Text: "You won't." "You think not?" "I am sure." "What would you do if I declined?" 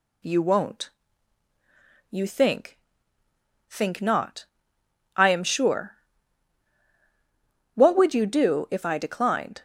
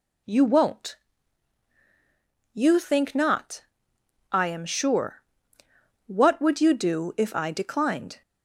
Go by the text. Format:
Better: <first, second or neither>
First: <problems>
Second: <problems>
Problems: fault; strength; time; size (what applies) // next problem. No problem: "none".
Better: second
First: says "think" twice; at 3.6 s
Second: none